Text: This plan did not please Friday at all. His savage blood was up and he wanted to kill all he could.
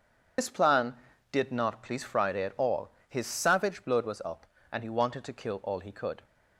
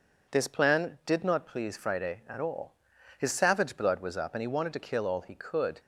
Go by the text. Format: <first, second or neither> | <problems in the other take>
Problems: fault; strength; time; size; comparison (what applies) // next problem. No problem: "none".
second | loses the start of "This"; at 0.3 s; 45 ms